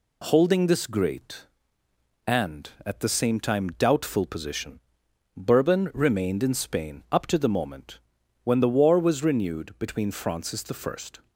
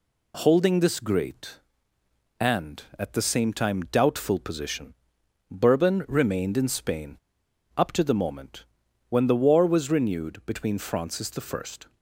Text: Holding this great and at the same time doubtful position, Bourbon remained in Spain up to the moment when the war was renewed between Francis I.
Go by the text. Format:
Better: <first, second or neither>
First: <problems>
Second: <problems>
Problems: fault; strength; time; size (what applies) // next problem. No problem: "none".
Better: first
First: pauses between "moment" and "when"; noticeable; at 7.9 s; 0.46 s long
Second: pauses between "Spain" and "up"; noticeable; at 7.1 s; 0.61 s long // pauses between "moment" and "when"; noticeable; at 8.6 s; 0.46 s long